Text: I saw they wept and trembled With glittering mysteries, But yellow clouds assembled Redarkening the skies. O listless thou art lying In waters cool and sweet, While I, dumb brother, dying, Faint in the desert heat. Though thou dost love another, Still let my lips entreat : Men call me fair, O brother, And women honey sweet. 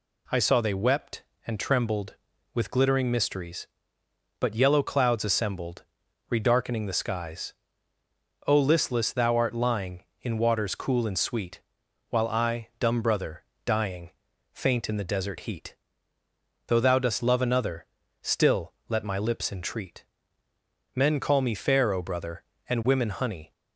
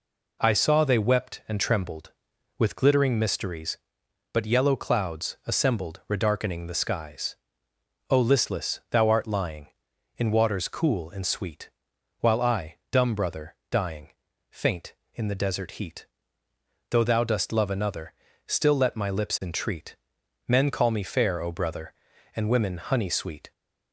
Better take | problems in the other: second | pauses between "assembled" and "Redarkening"; noticeable; at 5.8 s; 0.46 s long // pauses between "Still" and "let"; slight; at 18.7 s; 0.16 s long // stops before "sweet"; at 23.5 s

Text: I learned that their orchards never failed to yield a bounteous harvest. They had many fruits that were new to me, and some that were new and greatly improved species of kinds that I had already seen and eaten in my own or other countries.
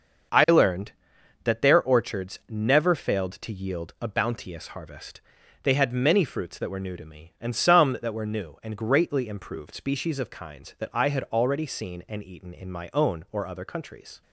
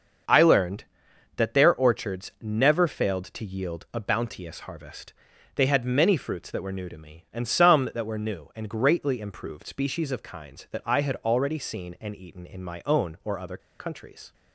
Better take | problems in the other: first | starts louder than the rest; until 1.8 s; 6.5 dB; also in the first // pauses between "other" and "countries"; slight; at 13.5 s; 0.21 s long

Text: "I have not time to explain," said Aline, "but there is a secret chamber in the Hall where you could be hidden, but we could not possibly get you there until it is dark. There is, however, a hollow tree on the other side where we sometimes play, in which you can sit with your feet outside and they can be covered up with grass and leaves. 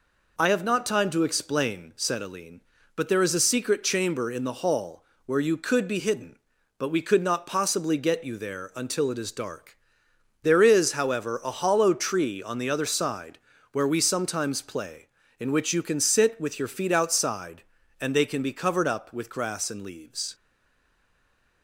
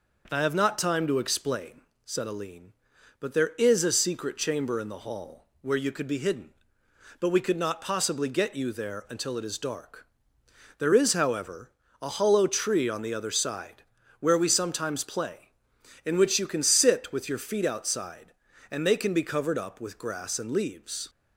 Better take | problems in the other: second | pauses between "Hall" and "where"; slight; at 5.0 s; 0.22 s long; slight in the second // pauses between "side" and "where"; slight; at 13.3 s; 0.32 s long; slight in the second // stays silent after the last word; noticeable; from 20.3 s on; 1.3 s long

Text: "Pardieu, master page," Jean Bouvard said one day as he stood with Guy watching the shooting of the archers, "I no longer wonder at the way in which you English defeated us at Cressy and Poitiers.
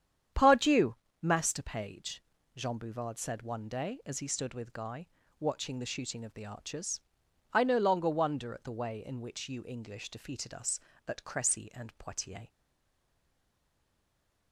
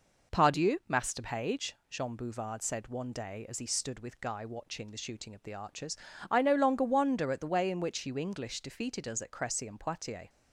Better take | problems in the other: second | starts louder than the rest; strong; until 1.6 s; 9 dB // pauses between "Guy" and "watching"; slight; at 5.0 s; 0.32 s long // stays silent after the last word; noticeable; from 12.4 s on; 2.1 s long

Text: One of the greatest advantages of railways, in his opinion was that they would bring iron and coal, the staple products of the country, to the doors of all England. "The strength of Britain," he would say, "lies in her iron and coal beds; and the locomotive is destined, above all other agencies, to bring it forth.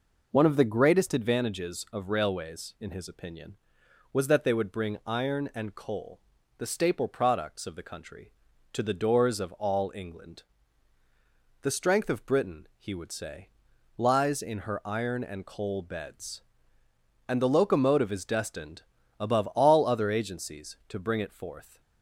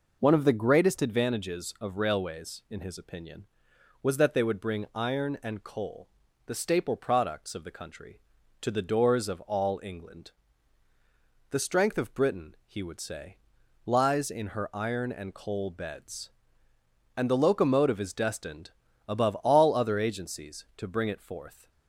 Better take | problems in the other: neither | none

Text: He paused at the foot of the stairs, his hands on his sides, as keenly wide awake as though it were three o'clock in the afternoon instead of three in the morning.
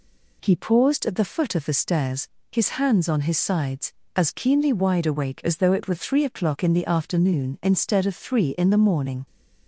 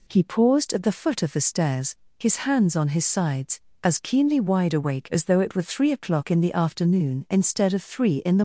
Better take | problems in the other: first | stops before "morning"; at 8.3 s

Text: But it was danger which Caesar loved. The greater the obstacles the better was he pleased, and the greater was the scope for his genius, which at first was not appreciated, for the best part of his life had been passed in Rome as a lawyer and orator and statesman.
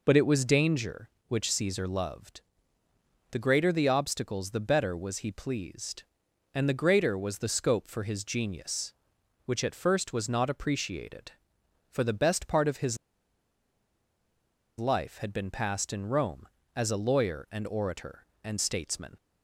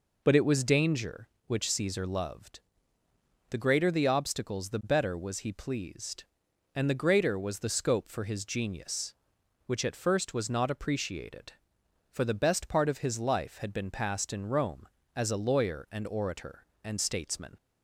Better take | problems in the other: second | pauses between "his" and "life"; strong; at 12.9 s; 1.8 s long

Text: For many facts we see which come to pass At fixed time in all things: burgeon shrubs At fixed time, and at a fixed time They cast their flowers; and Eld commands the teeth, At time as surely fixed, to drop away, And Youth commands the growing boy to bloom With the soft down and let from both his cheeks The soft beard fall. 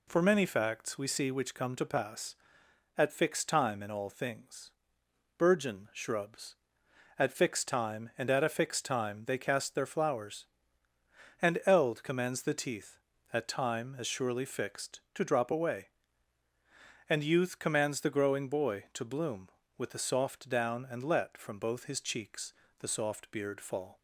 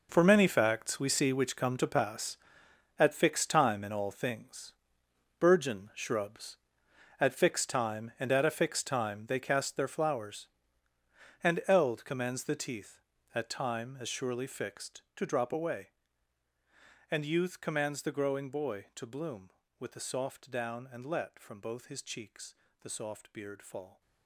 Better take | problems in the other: first | gets quieter; strong; throughout; 13.5 dB // pauses between "cheeks" and "The"; slight; at 22.5 s; 0.24 s long; slight in the first

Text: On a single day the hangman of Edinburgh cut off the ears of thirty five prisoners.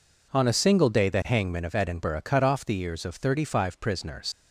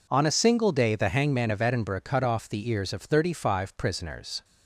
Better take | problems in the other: second | leaves "prisoners" unfinished; at 4.3 s; 105 ms

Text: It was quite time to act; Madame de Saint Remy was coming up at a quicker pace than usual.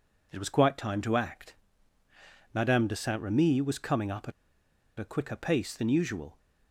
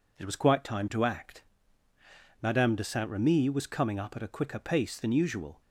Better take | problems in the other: second | pauses between "at" and "a"; noticeable; at 4.3 s; 0.67 s long

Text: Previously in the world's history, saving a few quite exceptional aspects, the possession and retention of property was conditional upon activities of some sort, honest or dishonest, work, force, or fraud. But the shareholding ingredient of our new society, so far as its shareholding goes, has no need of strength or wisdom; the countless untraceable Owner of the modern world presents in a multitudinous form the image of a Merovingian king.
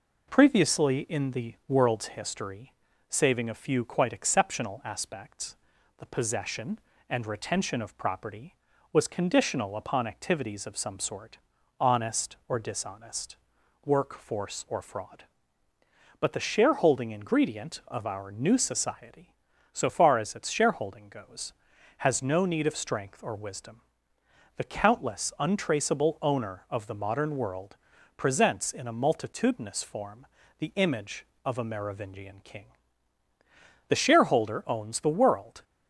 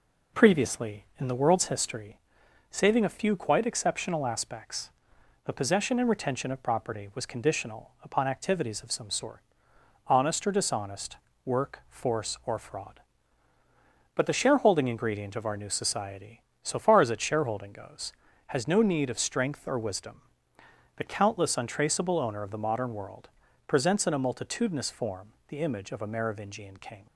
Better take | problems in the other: second | pauses between "world" and "presents"; at 27.7 s; 0.40 s long; also in the second // pauses between "form" and "the"; slight; at 30.2 s; 0.32 s long // goes on to say "The shareholder owns the world"; strong; from 33.8 s on; 1.7 s long

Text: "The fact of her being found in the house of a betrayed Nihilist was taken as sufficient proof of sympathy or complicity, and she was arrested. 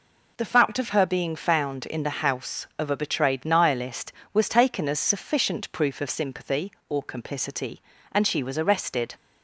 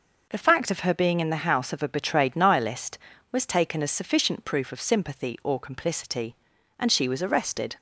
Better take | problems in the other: first | skips "found"; at 1.1 s

